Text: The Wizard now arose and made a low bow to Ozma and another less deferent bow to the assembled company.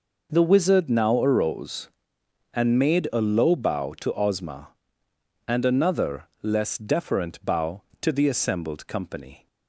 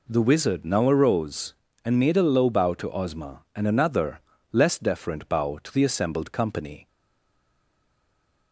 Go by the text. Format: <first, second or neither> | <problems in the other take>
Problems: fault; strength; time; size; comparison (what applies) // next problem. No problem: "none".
first | pauses between "another" and "less"; slight; at 4.2 s; 0.32 s long // stays silent after the last word; noticeable; from 6.8 s on; 1.7 s long